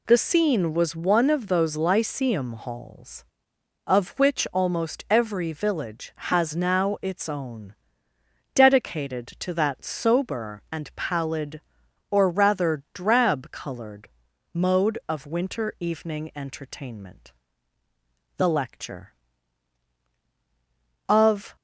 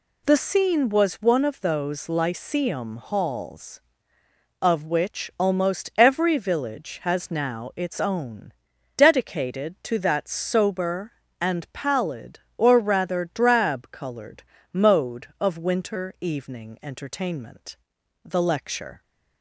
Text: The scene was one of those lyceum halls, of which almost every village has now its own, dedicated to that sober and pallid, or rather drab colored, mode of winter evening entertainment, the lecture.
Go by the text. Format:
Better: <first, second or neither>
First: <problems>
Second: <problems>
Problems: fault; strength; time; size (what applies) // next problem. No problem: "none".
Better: second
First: goes on to say "Of"; slight; from 21.0 s on; 0.48 s long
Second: none